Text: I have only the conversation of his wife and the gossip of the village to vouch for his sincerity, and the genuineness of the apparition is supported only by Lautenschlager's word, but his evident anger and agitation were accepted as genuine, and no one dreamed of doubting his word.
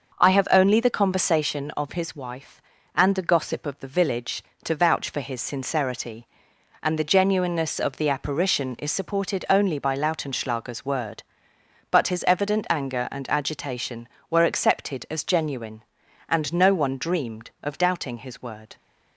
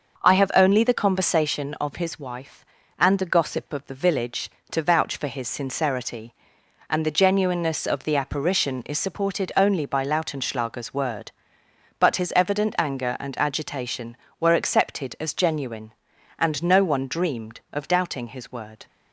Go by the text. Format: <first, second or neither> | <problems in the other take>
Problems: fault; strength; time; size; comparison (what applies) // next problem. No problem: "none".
neither | starts louder than the rest; the same in both